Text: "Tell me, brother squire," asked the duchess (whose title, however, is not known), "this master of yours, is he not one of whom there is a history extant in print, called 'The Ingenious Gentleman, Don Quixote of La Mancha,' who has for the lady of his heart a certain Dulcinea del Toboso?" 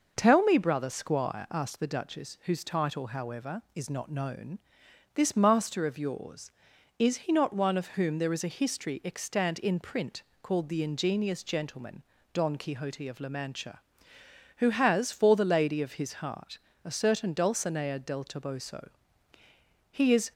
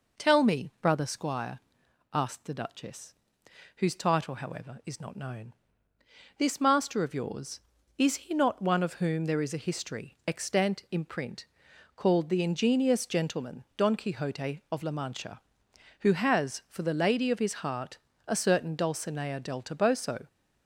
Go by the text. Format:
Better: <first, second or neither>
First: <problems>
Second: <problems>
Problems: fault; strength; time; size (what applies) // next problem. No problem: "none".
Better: second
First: pauses between "heart" and "a"; slight; at 16.5 s; 0.26 s long // goes on to say "He is"; slight; from 19.8 s on; 0.42 s long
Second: pauses between "heart" and "a"; slight; at 17.9 s; 0.30 s long